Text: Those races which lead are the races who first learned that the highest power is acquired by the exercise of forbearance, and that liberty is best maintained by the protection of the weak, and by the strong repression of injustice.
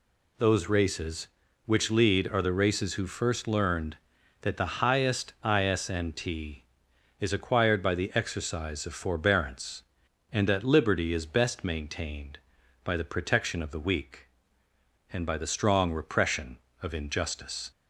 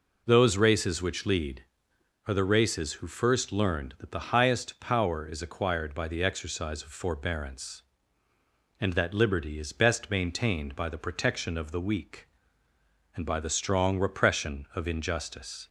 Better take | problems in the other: second | says "isnt" for "power"; at 5.4 s

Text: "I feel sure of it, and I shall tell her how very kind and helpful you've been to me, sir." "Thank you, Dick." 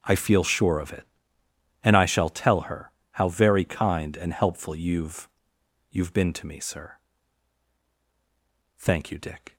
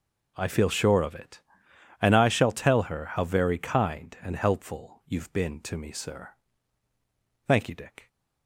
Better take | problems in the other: second | starts louder than the rest; until 1.0 s; 6.5 dB // pauses between "her" and "how"; slight; at 2.9 s; 0.20 s long // says "you've" twice; at 5.8 s

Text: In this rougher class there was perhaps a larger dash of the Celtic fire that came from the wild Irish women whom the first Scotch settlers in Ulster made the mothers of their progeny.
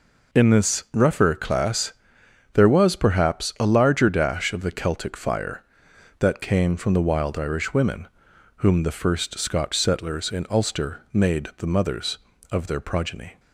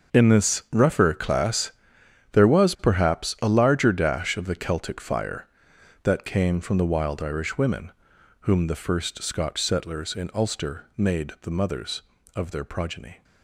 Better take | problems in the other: first | gets quieter; strong; throughout; 13 dB // pauses between "class" and "there"; noticeable; at 1.6 s; 0.62 s long; noticeable in the first // pauses between "women" and "whom"; noticeable; at 7.9 s; 0.50 s long; noticeable in the first

